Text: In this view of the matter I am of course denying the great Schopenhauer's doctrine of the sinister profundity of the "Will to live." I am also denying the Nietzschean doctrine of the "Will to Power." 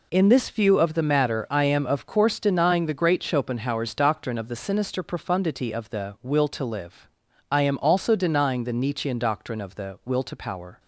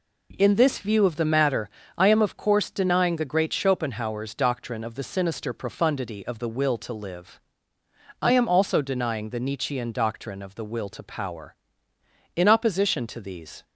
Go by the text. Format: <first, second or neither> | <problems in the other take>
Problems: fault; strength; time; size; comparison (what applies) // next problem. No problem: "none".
first | pauses between "matter" and "I"; slight; at 1.6 s; 0.28 s long // goes on to say "In opposition to these"; noticeable; from 12.3 s on; 1.2 s long